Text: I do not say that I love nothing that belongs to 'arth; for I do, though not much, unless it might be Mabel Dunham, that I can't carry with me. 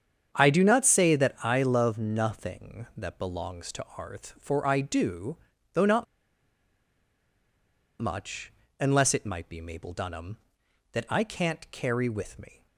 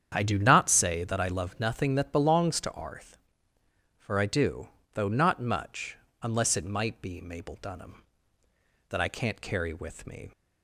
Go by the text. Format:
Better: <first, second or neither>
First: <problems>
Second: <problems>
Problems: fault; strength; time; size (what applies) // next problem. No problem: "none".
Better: second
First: starts louder than the rest; strong; until 1.3 s; 8 dB // pauses between "not" and "much"; strong; at 6.0 s; 1.9 s long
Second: starts louder than the rest; strong; until 1.1 s; 8.5 dB